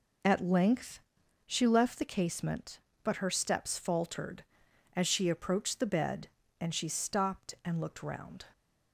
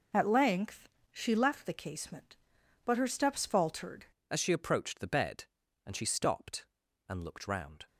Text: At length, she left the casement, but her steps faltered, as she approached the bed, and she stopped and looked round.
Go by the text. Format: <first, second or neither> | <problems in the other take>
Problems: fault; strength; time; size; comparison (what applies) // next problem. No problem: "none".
first | changes voice at "as"; from 4.3 s on; 3.5 s long